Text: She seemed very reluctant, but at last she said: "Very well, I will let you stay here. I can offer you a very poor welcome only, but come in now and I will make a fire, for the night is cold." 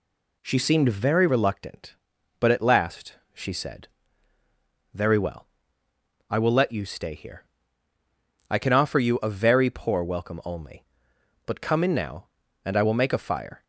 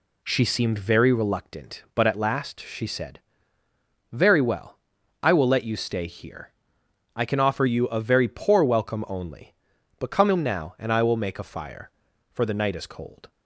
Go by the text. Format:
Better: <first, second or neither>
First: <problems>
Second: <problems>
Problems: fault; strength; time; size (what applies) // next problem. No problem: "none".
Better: second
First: pauses between "last" and "she"; slight; at 3.1 s; 0.18 s long // stops before "for the night is cold"; at 13.6 s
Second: none